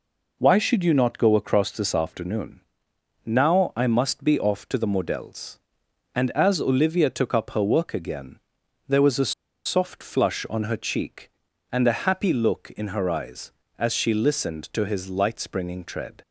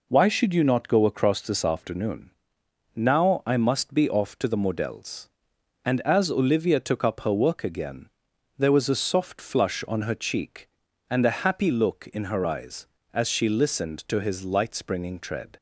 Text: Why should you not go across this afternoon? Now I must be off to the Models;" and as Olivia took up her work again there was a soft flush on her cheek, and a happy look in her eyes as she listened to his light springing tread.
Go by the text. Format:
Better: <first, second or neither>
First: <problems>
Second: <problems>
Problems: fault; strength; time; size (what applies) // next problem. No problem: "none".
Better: second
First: pauses between "again" and "there"; noticeable; at 8.3 s; 0.50 s long // pauses between "a" and "soft"; slight; at 9.3 s; 0.31 s long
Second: pauses between "again" and "there"; noticeable; at 8.0 s; 0.50 s long